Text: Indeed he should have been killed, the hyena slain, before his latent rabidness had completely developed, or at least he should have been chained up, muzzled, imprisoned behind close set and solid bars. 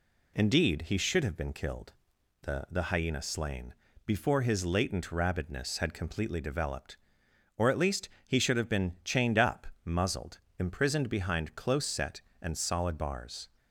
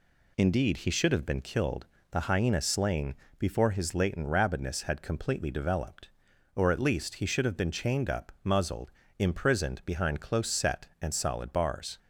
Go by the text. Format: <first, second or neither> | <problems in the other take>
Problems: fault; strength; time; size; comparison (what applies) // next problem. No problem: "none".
second | says "the" twice; at 2.6 s // pauses between "least" and "he"; slight; at 8.0 s; 0.18 s long